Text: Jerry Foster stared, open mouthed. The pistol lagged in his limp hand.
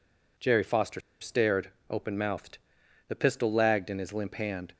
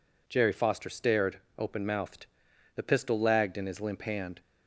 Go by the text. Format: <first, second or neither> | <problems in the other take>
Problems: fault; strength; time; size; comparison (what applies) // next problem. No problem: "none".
second | pauses between "Foster" and "stared"; slight; at 1.0 s; 0.20 s long